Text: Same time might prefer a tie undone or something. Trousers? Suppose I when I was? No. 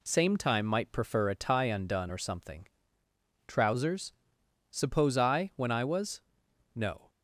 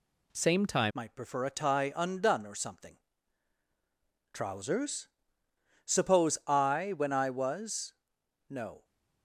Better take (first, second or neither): first